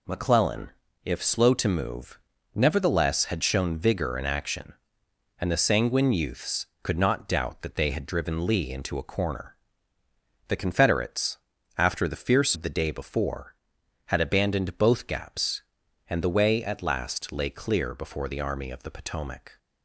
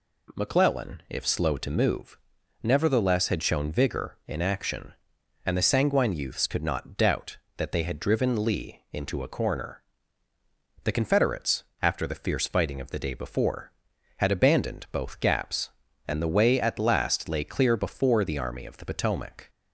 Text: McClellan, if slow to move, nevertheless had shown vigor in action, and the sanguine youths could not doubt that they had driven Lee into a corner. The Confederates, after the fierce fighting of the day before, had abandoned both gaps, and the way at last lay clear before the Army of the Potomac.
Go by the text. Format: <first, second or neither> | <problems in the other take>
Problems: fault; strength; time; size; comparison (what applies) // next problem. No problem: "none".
second | skips "fighting"; at 12.5 s